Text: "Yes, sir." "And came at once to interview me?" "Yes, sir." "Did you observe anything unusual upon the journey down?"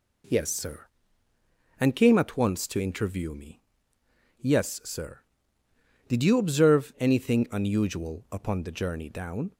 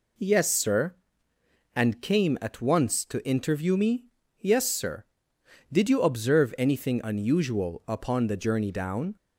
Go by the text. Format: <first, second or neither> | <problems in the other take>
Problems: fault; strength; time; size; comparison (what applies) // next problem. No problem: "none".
neither | none